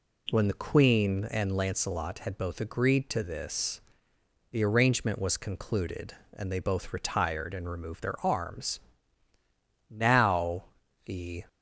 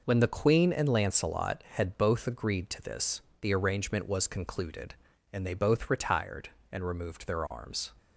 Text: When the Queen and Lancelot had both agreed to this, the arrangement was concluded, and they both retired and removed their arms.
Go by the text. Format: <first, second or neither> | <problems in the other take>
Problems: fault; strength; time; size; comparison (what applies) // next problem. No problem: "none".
second | goes on to say "Now the"; from 9.8 s on; 1.5 s long